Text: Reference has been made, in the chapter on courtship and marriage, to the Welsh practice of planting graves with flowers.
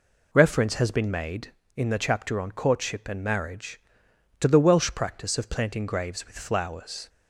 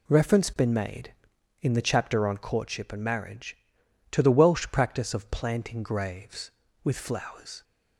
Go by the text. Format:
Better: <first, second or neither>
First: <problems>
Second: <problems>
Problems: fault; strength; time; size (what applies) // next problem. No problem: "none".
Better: first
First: none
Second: skips "has"; at 0.5 s